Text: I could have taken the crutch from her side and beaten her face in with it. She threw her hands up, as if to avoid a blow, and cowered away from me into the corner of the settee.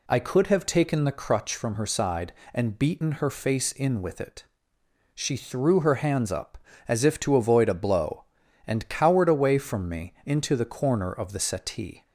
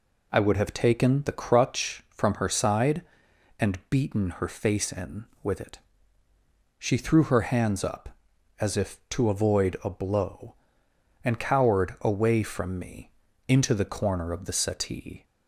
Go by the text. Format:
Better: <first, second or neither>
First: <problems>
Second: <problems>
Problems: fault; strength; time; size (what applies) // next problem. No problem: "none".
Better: first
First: none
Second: says "would" for "could"; at 0.3 s // pauses between "me" and "into"; at 13.1 s; 0.38 s long